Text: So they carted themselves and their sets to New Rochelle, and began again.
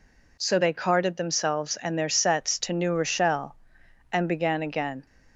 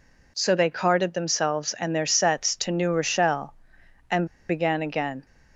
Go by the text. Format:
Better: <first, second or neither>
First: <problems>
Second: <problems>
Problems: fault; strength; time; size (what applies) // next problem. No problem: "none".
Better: first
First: none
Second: pauses between "and" and "began"; slight; at 4.2 s; 0.23 s long